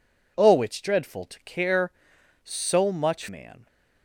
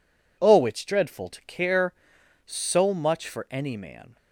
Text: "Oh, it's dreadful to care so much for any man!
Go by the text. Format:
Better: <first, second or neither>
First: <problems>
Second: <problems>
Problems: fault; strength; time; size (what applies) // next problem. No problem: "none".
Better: second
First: skips "for any"; at 3.2 s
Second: none